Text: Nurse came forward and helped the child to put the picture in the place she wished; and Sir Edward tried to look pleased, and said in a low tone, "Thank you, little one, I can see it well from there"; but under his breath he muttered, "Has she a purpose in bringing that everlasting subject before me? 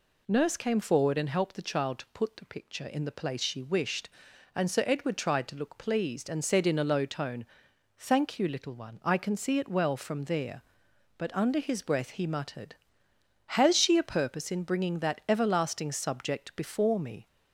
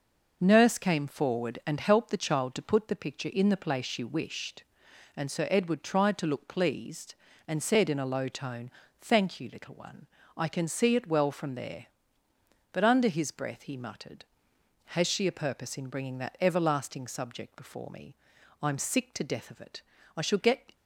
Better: first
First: none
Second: goes on to say "I'm sick to death of it I shall get"; strong; from 18.6 s on; 2.1 s long

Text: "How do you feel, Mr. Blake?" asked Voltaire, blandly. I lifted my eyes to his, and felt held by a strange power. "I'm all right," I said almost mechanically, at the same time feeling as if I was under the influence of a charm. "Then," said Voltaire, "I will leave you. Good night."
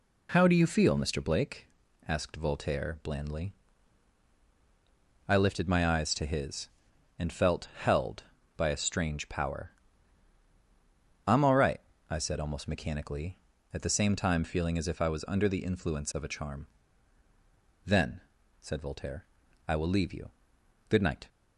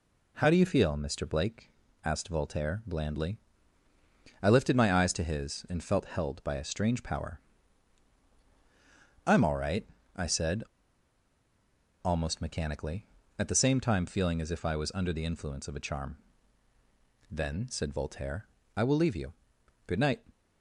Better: first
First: none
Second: pauses between "said" and "almost"; strong; at 10.6 s; 1.4 s long

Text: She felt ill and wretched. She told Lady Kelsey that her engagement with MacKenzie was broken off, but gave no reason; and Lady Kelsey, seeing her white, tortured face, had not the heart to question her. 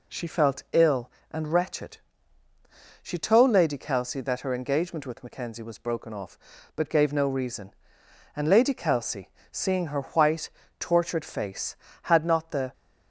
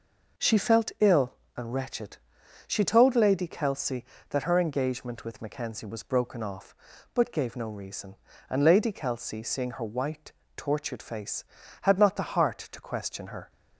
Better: second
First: stops before "heart to question her"; at 12.7 s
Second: none

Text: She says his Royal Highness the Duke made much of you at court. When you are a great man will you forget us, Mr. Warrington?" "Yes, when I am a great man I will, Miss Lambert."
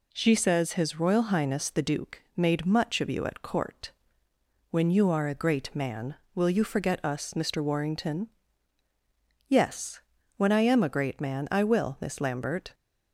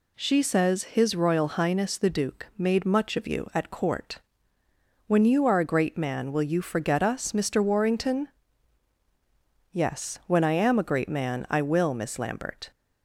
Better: neither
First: none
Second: none

